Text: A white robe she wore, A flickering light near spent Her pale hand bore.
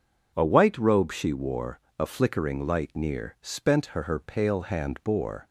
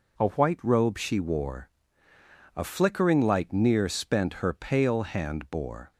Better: second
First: says "Her" twice; at 4.0 s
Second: none

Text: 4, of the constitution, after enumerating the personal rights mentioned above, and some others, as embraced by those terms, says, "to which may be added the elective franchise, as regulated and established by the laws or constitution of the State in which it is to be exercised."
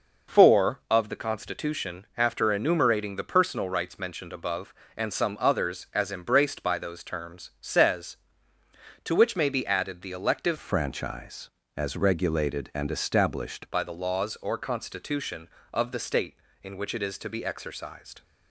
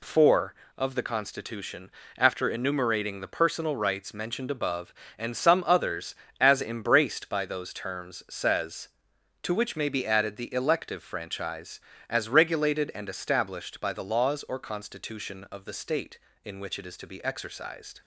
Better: second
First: changes voice from "franchise" to "established"; from 10.5 to 13.6 s; 3.1 s long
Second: none

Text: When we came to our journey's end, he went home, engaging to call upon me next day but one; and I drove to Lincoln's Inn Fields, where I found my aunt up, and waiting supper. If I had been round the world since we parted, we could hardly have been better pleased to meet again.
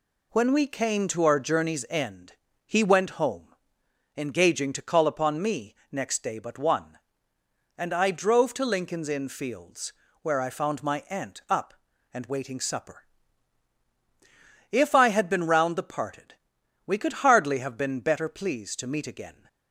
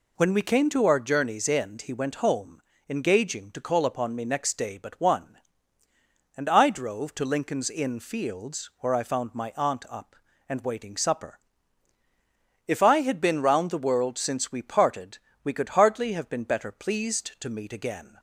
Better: second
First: pauses between "me" and "next"; slight; at 5.7 s; 0.16 s long // skips "world since we"; at 15.8 s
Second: none

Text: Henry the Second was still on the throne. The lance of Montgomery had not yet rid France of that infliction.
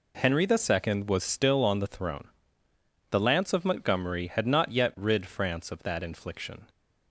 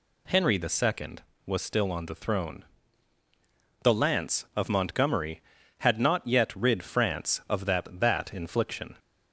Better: first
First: none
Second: says "that" twice; at 8.0 s

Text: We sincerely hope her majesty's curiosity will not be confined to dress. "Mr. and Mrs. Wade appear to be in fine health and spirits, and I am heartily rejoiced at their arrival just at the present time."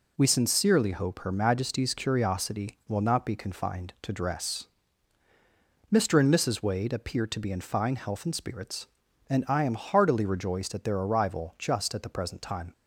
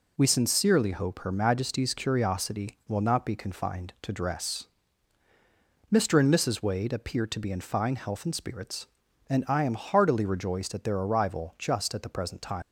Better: first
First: none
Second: leaves "time" unfinished; at 12.6 s; 100 ms

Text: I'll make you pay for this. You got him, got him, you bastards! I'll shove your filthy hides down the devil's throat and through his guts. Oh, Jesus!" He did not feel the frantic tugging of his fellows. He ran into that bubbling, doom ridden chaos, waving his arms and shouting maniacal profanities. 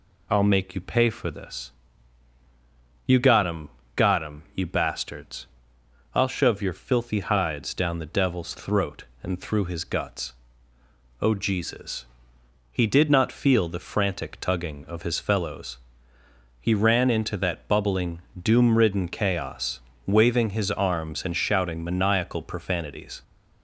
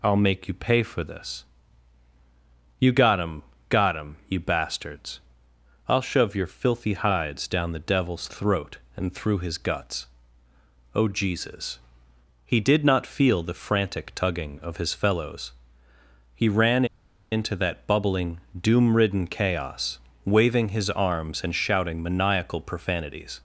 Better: first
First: none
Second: pauses between "ran" and "into"; noticeable; at 16.8 s; 0.46 s long

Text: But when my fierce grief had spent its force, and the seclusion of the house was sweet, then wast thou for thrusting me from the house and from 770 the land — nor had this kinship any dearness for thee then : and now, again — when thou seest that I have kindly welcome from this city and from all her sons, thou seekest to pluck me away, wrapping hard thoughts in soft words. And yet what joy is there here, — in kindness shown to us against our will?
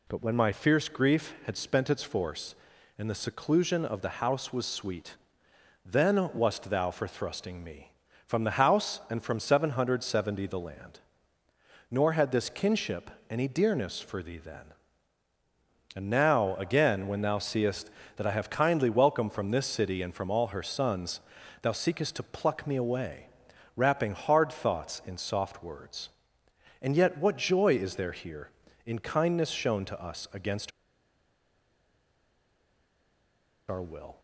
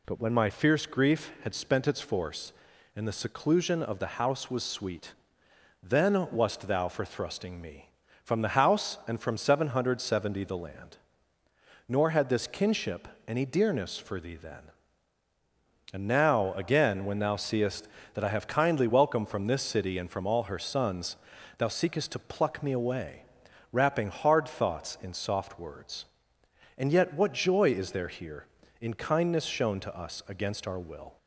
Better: second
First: pauses between "kinship" and "any"; slight; at 13.1 s; 0.20 s long // pauses between "against" and "our"; strong; at 30.7 s; 2.9 s long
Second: pauses between "kinship" and "any"; slight; at 13.0 s; 0.20 s long

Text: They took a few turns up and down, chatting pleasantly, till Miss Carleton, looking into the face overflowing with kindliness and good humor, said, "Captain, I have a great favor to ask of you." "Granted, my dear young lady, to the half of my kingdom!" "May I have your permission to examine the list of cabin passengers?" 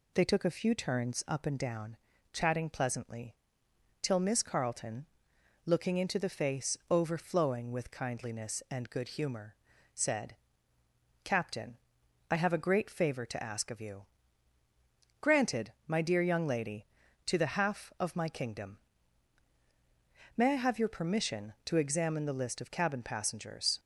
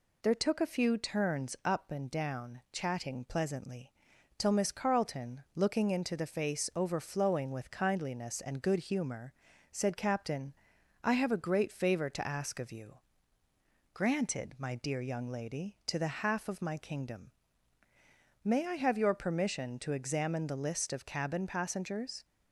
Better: first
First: none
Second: says "There" for "They"; at 0.2 s

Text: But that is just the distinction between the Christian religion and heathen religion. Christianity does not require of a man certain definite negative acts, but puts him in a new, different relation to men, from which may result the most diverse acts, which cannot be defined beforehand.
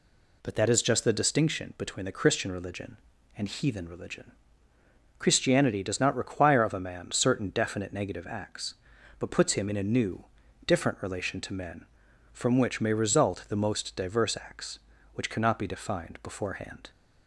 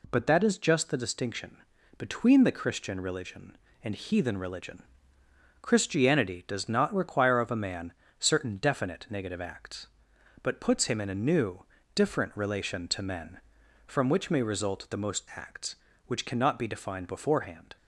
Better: first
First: none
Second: pauses between "distinction" and "between"; at 1.5 s; 0.40 s long // pauses between "man" and "certain"; slight; at 7.9 s; 0.28 s long // skips "diverse"; at 15.3 s

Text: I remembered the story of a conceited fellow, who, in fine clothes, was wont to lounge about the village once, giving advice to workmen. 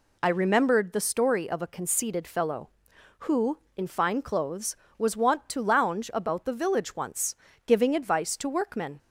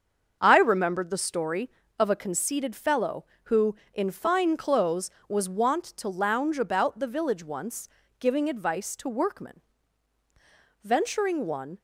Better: first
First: none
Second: starts louder than the rest; until 1.4 s; 7 dB // goes on to say "Venturing one"; noticeable; from 10.8 s on; 0.96 s long

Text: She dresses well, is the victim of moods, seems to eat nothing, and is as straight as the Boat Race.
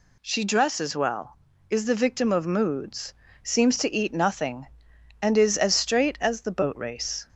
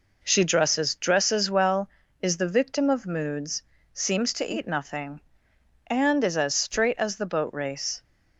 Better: first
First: none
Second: says "dresses" twice; at 0.9 s

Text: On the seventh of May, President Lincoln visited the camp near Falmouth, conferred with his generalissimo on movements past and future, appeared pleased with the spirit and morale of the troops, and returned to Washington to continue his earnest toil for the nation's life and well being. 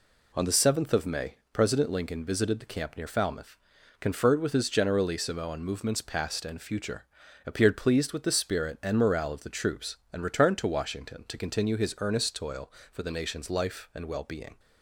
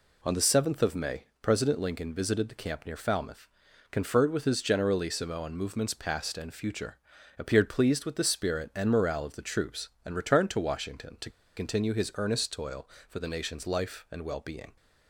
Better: first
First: none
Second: pauses between "to" and "continue"; slight; at 11.2 s; 0.26 s long

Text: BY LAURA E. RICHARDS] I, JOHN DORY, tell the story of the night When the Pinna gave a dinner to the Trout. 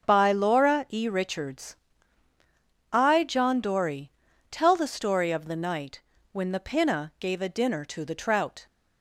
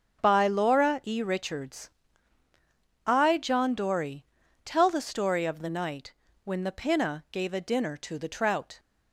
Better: neither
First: starts louder than the rest; until 1.1 s; 6.5 dB // pauses between "RICHARDS" and "I"; at 1.7 s; 1.1 s long // pauses between "night" and "When"; slight; at 6.0 s; 0.32 s long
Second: starts louder than the rest; until 1.2 s; 6.5 dB // pauses between "RICHARDS" and "I"; at 1.9 s; 1.1 s long // pauses between "night" and "When"; slight; at 6.1 s; 0.32 s long

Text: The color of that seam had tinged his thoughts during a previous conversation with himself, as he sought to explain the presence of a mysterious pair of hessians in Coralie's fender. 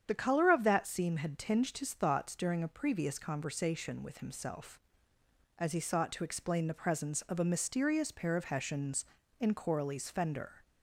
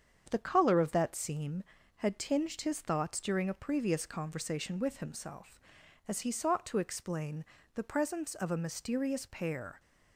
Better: first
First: starts louder than the rest; strong; until 1.0 s; 8.5 dB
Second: starts louder than the rest; strong; until 1.3 s; 7.5 dB // pauses between "explain" and "the"; slight; at 7.4 s; 0.30 s long // stops before "of hessians in Coralie's fender"; at 9.7 s

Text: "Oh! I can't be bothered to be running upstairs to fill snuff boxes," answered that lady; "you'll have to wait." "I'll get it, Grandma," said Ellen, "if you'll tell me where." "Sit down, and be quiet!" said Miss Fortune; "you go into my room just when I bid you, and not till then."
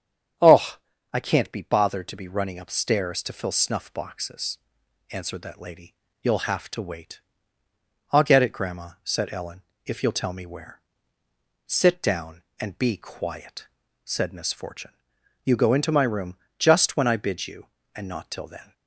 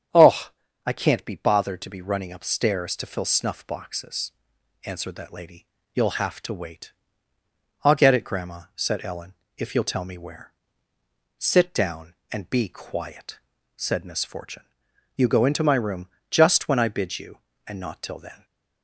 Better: neither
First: starts louder than the rest; strong; until 1.7 s; 8.5 dB // pauses between "room" and "just"; slight; at 16.3 s; 0.22 s long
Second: starts louder than the rest; strong; until 1.4 s; 8.5 dB // pauses between "room" and "just"; slight; at 16.0 s; 0.22 s long

